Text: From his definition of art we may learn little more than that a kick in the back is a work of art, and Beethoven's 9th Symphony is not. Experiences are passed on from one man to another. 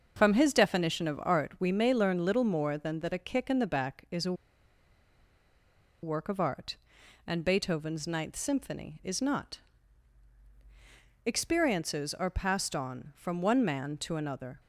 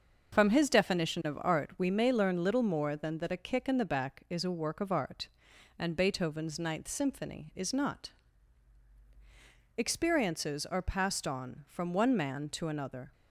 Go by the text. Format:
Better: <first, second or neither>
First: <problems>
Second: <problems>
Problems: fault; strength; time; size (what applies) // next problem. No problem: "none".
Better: second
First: starts louder than the rest; until 1.1 s; 6.5 dB // pauses between "a" and "work"; strong; at 4.3 s; 1.6 s long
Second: starts louder than the rest; until 1.3 s; 6.5 dB